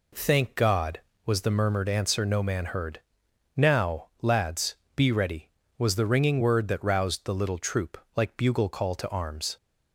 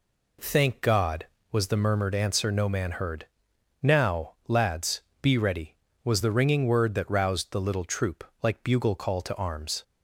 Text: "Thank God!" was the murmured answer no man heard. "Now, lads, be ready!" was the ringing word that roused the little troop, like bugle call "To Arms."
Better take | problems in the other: neither | none

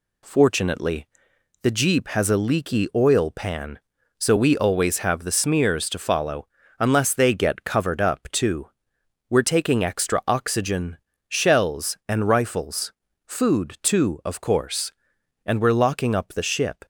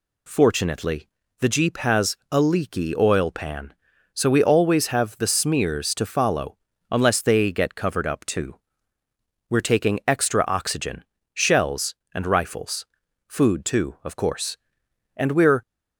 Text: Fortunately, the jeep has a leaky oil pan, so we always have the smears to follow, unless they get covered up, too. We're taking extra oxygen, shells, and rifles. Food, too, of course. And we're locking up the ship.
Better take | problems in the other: first | pauses between "has" and "a"; slight; at 2.1 s; 0.16 s long // stops before "locking up the ship"; at 15.6 s

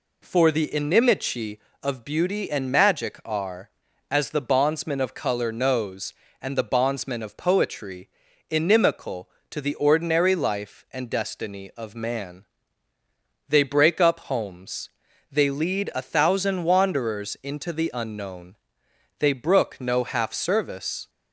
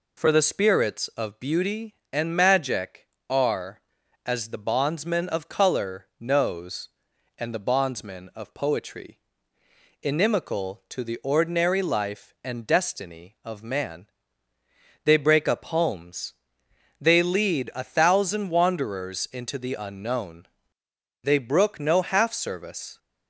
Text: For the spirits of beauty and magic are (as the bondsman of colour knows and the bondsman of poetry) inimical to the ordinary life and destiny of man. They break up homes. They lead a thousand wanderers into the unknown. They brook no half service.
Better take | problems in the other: second | says "inimici" for "spirits"; at 0.6 s

